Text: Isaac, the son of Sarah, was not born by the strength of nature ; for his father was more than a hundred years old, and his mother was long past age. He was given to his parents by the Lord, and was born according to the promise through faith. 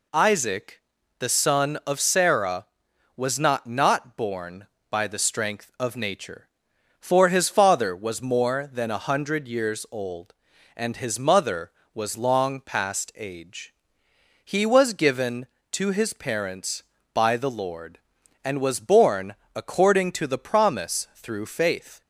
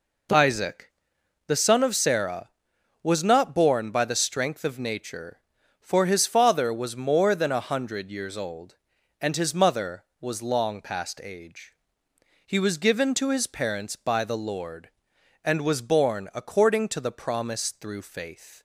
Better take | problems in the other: second | says "not" twice; at 3.6 s // pauses between "born" and "according"; slight; at 19.3 s; 0.20 s long

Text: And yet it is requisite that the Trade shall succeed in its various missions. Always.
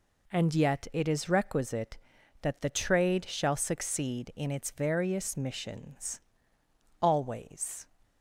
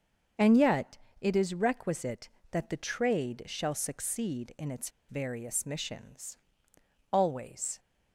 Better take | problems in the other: first | starts louder than the rest; until 1.6 s; 6.5 dB // pauses between "yet" and "it"; slight; at 0.9 s; 0.24 s long // pauses between "its" and "various"; slight; at 4.8 s; 0.19 s long

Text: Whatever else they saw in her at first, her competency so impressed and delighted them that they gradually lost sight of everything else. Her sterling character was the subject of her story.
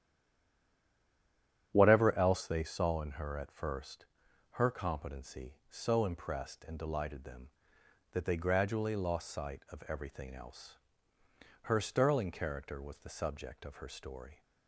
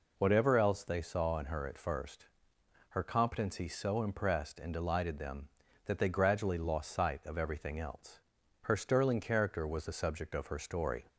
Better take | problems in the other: second | stays silent before the first word; noticeable; until 1.7 s; 1.7 s long // starts louder than the rest; strong; until 2.7 s; 9 dB

